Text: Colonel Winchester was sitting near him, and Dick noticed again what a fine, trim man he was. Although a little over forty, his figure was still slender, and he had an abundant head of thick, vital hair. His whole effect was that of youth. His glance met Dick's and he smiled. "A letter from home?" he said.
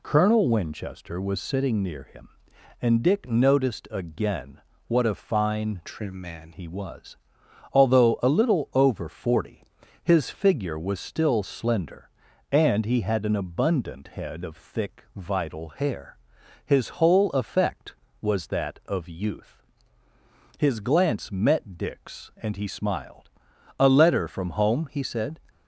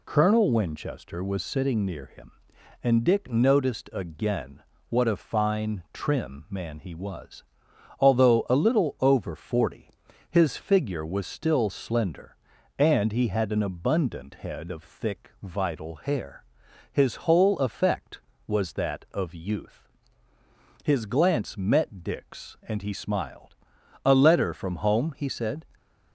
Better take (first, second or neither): second